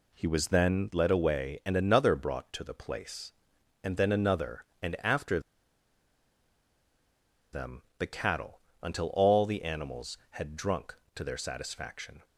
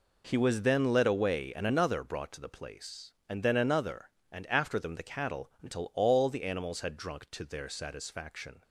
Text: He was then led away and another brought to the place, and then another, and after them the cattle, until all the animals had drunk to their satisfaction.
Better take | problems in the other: second | pauses between "after" and "them"; strong; at 5.3 s; 2.1 s long // pauses between "them" and "the"; slight; at 7.8 s; 0.16 s long

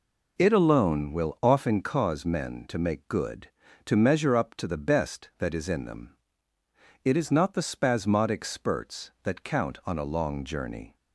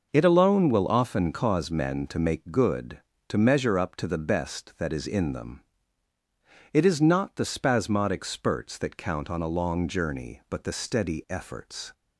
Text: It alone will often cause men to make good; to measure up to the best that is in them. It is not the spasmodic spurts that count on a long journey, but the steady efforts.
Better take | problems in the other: second | stops before "but the steady efforts"; at 10.9 s

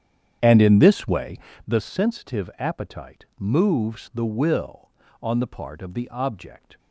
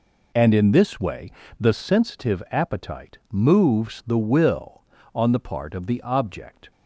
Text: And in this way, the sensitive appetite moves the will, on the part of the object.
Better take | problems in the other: second | starts louder than the rest; strong; until 1.7 s; 9 dB

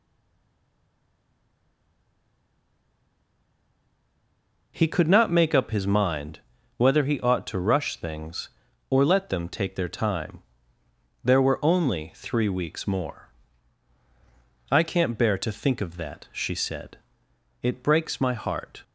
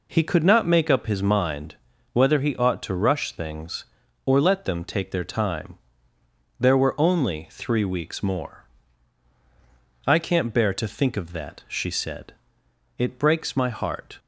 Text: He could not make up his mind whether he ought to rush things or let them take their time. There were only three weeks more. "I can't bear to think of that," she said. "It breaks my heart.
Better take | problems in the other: second | stays silent before the first word; strong; until 4.7 s; 4.7 s long // pauses between "mind" and "whether"; slight; at 6.4 s; 0.36 s long; slight in the second

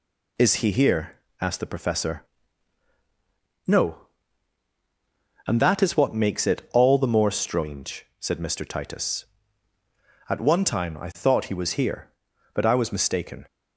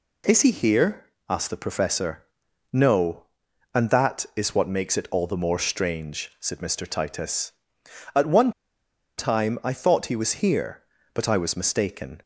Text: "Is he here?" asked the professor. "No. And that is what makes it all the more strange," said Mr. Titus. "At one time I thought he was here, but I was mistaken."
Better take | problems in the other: first | pauses between "one" and "time"; noticeable; at 8.5 s; 0.66 s long

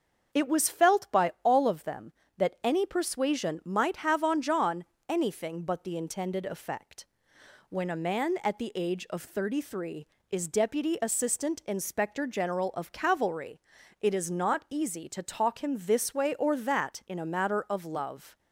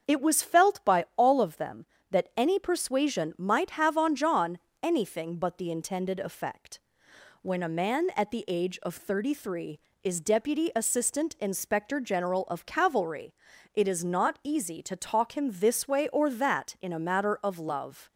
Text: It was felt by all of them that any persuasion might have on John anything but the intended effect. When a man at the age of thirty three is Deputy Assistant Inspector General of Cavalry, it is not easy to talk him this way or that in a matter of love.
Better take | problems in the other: neither | starts louder than the rest; the same in both // pauses between "John" and "anything"; slight; the same in both

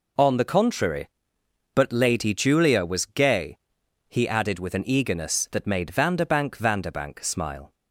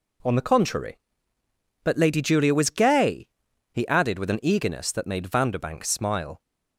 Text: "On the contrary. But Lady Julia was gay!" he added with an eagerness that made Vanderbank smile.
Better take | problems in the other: second | says "Vanderbank" twice; at 6.5 s

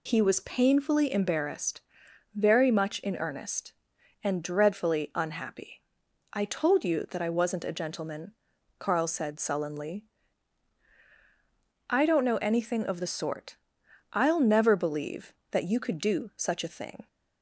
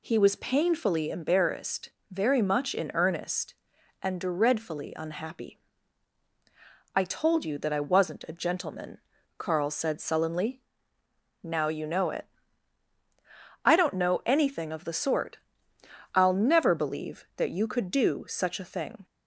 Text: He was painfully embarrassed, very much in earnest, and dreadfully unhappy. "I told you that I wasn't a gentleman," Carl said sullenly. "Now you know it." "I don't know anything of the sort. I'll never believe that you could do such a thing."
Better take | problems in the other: second | skips "Now you know it"; at 10.9 s

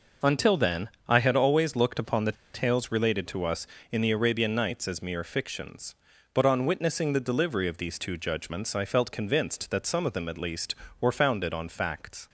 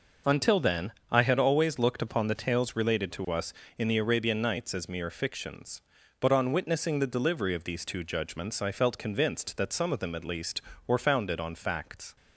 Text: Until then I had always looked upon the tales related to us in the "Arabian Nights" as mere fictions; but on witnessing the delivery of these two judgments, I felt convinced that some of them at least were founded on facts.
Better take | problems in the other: second | pauses between "then" and "I"; slight; at 0.8 s; 0.20 s long; slight in the second // pauses between "the" and "tales"; slight; at 2.3 s; 0.21 s long

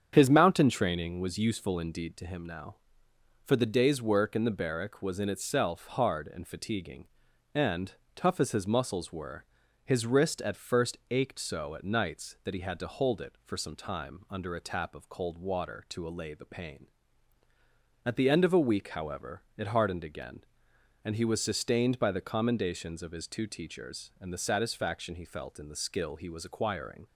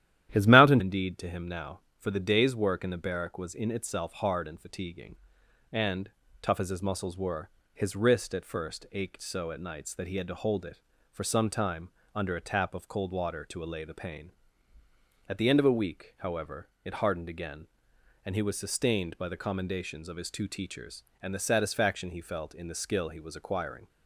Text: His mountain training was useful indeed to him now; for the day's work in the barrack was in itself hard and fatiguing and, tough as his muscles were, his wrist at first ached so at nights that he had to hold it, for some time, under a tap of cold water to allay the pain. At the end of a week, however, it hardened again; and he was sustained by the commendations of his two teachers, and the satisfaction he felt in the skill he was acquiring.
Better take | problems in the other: first | starts louder than the rest; strong; until 1.3 s; 12 dB; strong in the first // skips "training was useful"; at 0.7 s

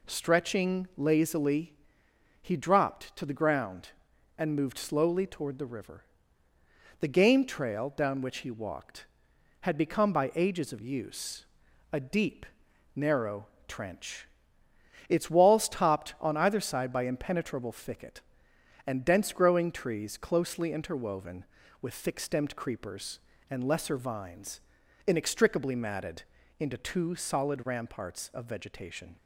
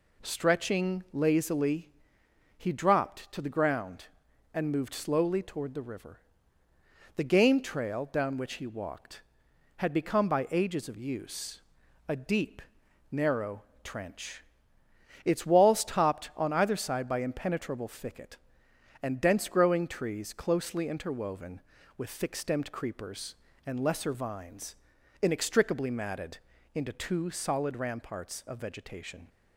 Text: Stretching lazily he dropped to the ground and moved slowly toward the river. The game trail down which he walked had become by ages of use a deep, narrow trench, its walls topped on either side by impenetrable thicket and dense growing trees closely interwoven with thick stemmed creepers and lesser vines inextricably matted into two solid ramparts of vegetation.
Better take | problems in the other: neither | pauses between "lazily" and "he"; noticeable; the same in both // pauses between "use" and "a"; the same in both // pauses between "narrow" and "trench"; slight; the same in both // pauses between "vines" and "inextricably"; noticeable; the same in both // pauses between "matted" and "into"; slight; the same in both

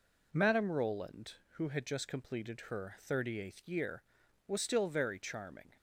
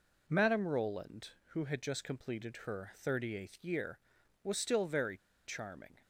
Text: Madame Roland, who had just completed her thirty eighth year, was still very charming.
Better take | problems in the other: first | pauses between "very" and "charming"; slight; at 5.1 s; 0.28 s long

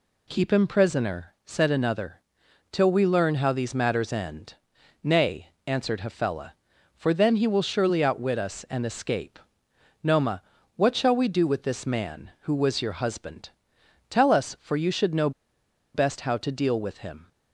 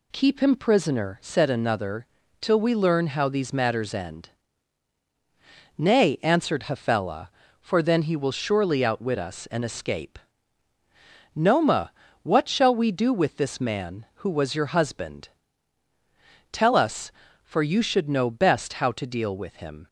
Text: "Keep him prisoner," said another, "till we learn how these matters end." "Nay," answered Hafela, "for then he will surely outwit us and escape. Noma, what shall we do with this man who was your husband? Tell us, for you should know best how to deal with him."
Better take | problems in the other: second | pauses between "know" and "best"; noticeable; at 15.3 s; 0.63 s long

